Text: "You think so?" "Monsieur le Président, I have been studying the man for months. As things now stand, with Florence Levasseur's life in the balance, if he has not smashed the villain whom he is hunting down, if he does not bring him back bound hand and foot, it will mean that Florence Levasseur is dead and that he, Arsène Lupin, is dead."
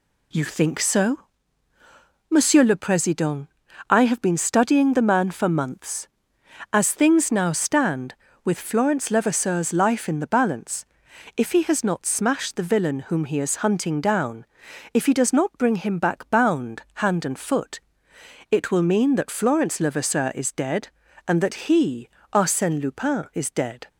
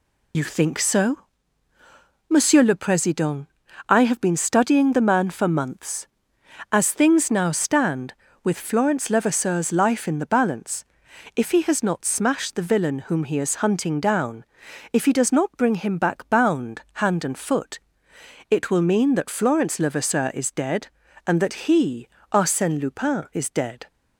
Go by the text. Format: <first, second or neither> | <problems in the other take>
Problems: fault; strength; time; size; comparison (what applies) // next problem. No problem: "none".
first | loses the start of "You"; at 0.3 s; 40 ms